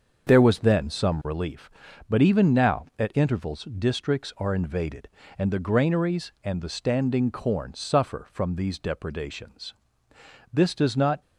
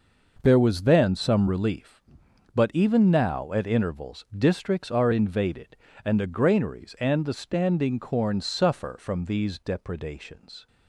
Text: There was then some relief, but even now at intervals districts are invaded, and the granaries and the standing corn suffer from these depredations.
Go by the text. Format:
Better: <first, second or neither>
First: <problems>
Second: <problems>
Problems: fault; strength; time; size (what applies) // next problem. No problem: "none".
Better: second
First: starts louder than the rest; until 1.3 s; 6.5 dB // goes on to say "This does not"; noticeable; from 10.5 s on; 0.68 s long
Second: none